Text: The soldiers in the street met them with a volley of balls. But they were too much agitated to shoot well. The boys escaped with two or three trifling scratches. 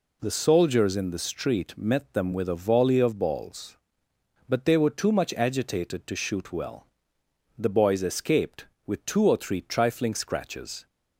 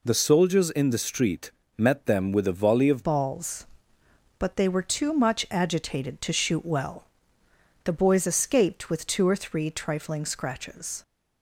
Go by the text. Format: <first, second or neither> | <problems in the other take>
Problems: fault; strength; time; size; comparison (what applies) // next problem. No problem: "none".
first | pauses between "street" and "met"; slight; at 1.5 s; 0.26 s long // changes voice at "balls"; from 3.0 s on; 8.0 s long